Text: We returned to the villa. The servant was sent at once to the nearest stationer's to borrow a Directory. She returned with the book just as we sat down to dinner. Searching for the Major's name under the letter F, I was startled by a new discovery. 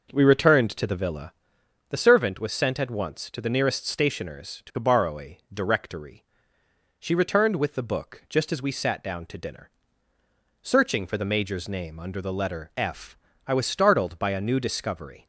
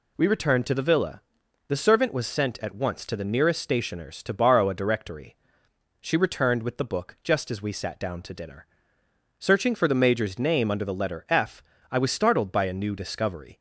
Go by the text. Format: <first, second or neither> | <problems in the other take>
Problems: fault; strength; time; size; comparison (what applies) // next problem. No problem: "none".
second | starts louder than the rest; noticeable; until 1.9 s; 6 dB